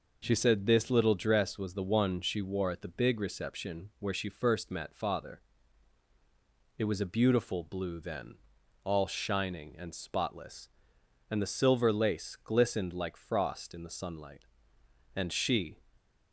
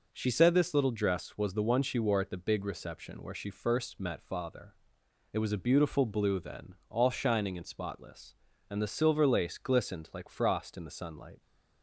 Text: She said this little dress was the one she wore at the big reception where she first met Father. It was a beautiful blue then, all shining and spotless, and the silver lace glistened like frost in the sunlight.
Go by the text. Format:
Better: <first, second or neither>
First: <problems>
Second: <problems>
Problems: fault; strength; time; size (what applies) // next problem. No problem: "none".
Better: second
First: goes on to say "And she"; noticeable; from 15.1 s on; 0.62 s long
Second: none